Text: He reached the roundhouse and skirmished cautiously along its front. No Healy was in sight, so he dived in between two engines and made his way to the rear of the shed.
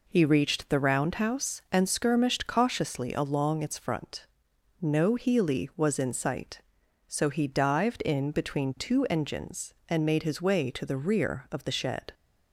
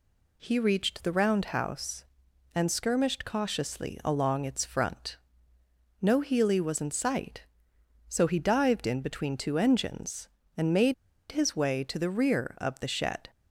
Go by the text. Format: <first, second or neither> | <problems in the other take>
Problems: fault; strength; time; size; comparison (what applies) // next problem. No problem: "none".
first | pauses between "made" and "his"; at 10.9 s; 0.37 s long